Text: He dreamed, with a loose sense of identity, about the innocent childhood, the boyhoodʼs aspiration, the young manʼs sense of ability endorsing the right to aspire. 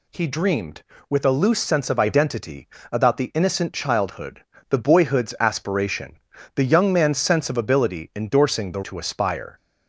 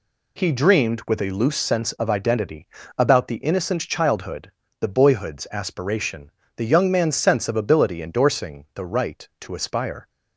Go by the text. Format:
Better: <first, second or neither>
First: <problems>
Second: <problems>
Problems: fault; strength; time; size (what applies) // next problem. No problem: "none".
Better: second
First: skips "right"; at 8.8 s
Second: none